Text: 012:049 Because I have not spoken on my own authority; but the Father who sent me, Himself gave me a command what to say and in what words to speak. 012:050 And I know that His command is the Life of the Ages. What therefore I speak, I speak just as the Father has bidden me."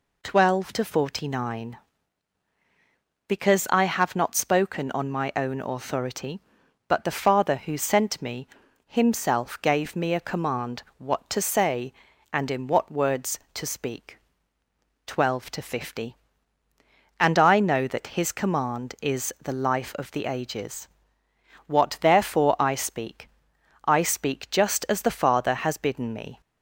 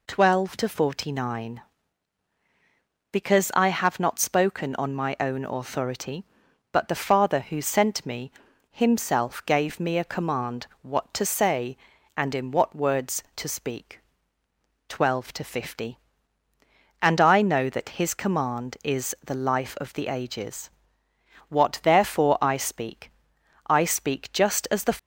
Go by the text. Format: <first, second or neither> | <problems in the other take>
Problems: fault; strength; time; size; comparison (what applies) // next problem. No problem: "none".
first | pauses between "command" and "what"; slight; at 10.6 s; 0.16 s long; slight in the first // stops before "Father has bidden me"; at 24.9 s